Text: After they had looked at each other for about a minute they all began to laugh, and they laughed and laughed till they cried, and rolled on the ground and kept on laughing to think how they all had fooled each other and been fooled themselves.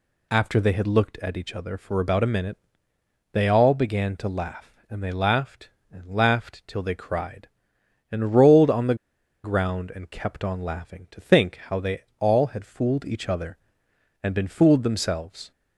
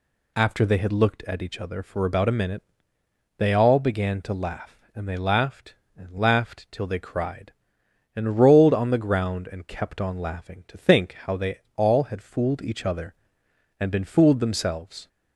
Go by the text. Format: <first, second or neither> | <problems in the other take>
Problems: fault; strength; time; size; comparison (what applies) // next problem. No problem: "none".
second | pauses between "minute" and "they"; noticeable; at 2.5 s; 0.76 s long; noticeable in the second // pauses between "the" and "ground"; noticeable; at 8.9 s; 0.49 s long // pauses between "they" and "all"; slight; at 12.0 s; 0.16 s long; slight in the second